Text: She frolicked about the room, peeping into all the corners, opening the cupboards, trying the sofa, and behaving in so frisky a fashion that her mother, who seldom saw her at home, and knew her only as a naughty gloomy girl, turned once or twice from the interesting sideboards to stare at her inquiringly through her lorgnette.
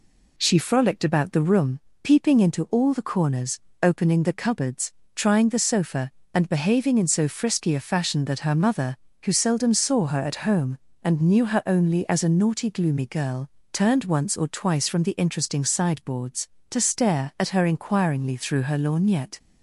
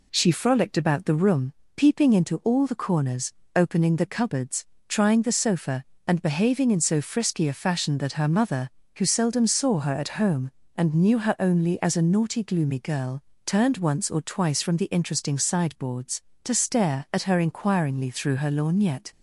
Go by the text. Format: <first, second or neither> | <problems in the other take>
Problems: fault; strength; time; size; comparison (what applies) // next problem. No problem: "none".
neither | none